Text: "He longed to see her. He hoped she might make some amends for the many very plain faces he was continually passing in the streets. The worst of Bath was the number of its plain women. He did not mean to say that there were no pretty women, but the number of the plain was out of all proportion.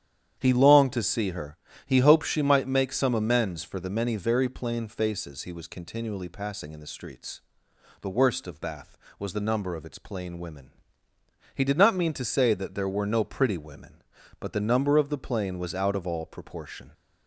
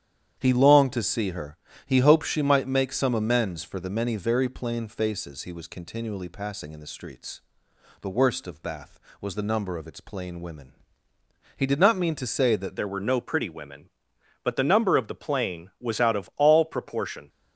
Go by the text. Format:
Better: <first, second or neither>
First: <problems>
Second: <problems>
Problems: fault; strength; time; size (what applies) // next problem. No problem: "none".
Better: first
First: starts louder than the rest; strong; until 1.3 s; 9.5 dB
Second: starts louder than the rest; strong; until 1.3 s; 9.5 dB // changes voice at "there"; from 12.7 s on; 4.5 s long